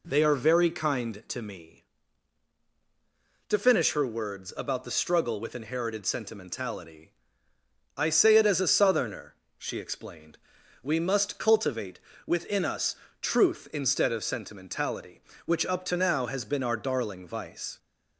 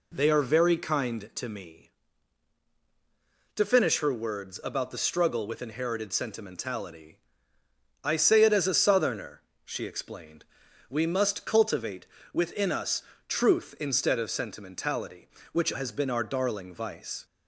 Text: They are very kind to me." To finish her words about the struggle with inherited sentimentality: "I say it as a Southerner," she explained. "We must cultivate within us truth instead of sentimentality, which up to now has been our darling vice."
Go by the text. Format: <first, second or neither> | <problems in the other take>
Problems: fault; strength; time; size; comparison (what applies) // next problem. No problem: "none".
first | pauses between "cultivate" and "within"; slight; at 12.0 s; 0.26 s long; slight in the first // pauses between "us" and "truth"; slight; at 13.0 s; 0.26 s long; slight in the first // skips "up to now"; at 15.7 s